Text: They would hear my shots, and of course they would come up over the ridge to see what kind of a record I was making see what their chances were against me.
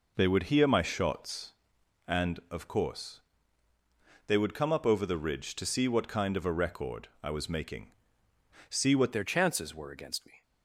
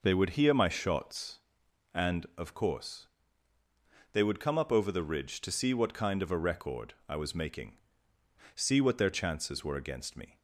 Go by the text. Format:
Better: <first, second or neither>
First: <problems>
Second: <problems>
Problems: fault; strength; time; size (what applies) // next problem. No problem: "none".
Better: second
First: pauses between "course" and "they"; at 3.2 s; 1.0 s long // pauses between "making" and "see"; noticeable; at 7.9 s; 0.78 s long // changes voice at "their"; from 9.1 s on; 1.3 s long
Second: pauses between "course" and "they"; at 3.0 s; 1.0 s long // pauses between "making" and "see"; noticeable; at 7.7 s; 0.78 s long